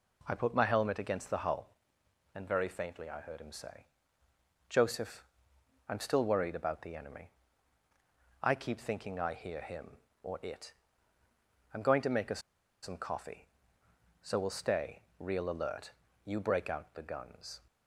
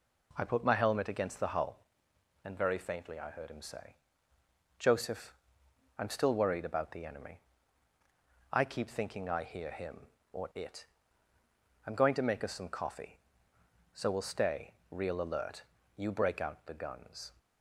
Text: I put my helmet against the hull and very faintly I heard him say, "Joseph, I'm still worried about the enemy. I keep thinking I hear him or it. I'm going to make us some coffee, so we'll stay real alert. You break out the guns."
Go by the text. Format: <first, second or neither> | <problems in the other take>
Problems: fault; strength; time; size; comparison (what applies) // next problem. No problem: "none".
second | pauses between "us" and "some"; at 12.3 s; 0.42 s long // pauses between "stay" and "real"; slight; at 15.0 s; 0.18 s long; slight in the second